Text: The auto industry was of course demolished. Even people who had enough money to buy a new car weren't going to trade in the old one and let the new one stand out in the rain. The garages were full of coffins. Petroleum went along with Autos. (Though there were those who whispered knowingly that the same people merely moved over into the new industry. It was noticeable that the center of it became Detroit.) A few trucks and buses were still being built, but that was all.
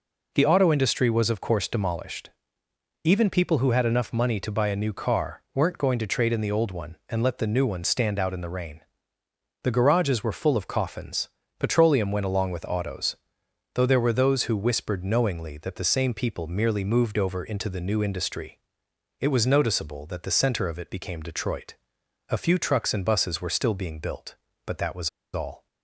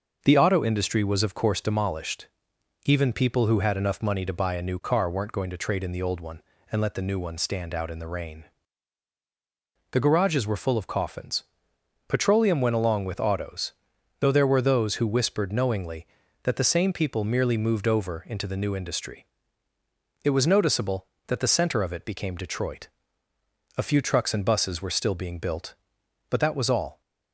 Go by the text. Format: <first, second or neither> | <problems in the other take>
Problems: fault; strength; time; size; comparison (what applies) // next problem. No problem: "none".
second | pauses between "was" and "all"; slight; at 25.0 s; 0.24 s long